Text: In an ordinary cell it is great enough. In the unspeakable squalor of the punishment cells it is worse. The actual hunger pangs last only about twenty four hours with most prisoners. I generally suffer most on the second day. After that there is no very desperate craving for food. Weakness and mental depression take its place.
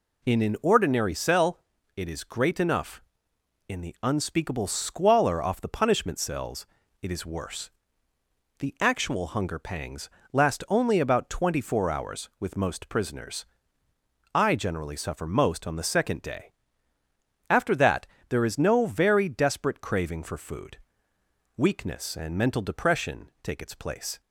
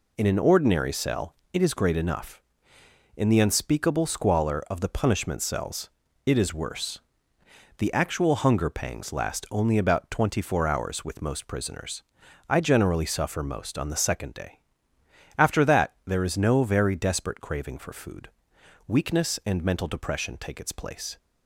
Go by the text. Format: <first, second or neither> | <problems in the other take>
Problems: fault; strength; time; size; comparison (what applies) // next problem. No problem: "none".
second | pauses between "cell" and "it"; at 1.5 s; 0.38 s long; slight in the second // says "off" for "of"; at 5.4 s // pauses between "cells" and "it"; at 6.6 s; 0.38 s long; slight in the second // pauses between "pangs" and "last"; slight; at 10.0 s; 0.24 s long // pauses between "that" and "there"; slight; at 18.0 s; 0.22 s long